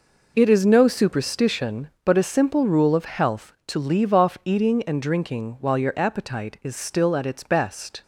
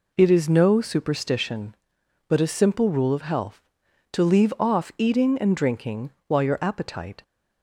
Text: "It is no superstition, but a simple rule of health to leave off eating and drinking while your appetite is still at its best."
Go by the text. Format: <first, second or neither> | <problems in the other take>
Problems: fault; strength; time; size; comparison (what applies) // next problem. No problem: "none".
first | pauses between "drinking" and "while"; slight; at 6.1 s; 0.16 s long // stops before "is still at its best"; at 7.2 s